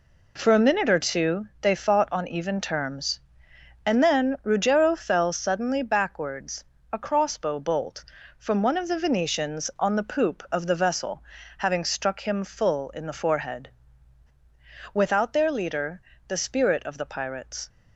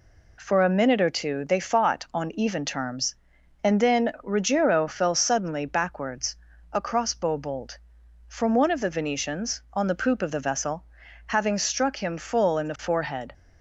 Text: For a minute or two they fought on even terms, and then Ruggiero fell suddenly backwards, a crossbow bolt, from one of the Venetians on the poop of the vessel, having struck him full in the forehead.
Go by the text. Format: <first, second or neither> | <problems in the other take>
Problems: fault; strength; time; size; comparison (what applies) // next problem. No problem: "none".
second | goes on to say "Without their leader the spirit of the pirates"; strong; from 14.9 s on; 2.7 s long